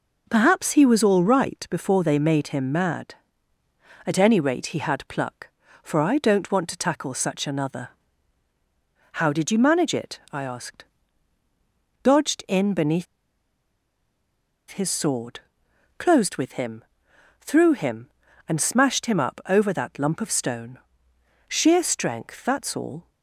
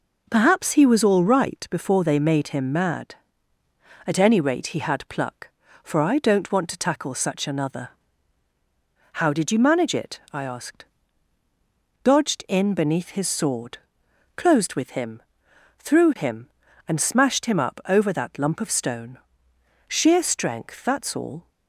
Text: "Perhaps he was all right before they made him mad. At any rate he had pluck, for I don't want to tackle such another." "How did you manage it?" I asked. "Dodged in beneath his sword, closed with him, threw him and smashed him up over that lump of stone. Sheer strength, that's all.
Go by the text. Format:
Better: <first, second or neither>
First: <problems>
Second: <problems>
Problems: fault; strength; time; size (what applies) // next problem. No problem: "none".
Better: second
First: pauses between "beneath" and "his"; strong; at 13.0 s; 1.6 s long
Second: none